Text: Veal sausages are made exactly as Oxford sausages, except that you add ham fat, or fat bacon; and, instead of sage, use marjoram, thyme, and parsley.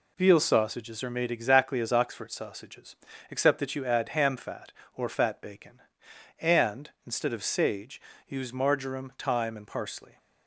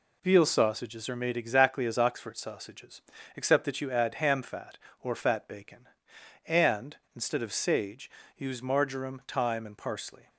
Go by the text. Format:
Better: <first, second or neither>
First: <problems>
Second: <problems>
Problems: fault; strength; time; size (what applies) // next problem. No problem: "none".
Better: neither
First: none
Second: none